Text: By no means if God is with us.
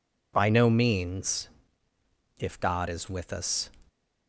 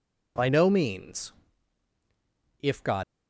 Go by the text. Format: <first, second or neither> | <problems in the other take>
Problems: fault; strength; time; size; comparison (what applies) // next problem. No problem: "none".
first | pauses between "means" and "if"; strong; at 1.3 s; 1.2 s long; noticeable in the first // stops before "is with us"; at 3.0 s